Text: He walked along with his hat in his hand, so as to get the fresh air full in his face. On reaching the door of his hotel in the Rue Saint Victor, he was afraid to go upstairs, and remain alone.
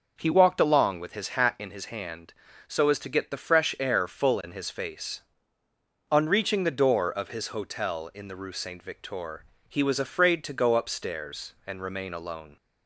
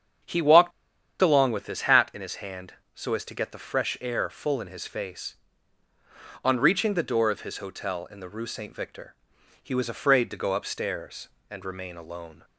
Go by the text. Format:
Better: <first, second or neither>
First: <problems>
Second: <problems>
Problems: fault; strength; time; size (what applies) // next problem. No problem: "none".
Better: first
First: starts louder than the rest; until 1.1 s; 6 dB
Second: starts louder than the rest; strong; until 1.7 s; 7.5 dB // pauses between "walked" and "along"; noticeable; at 0.7 s; 0.51 s long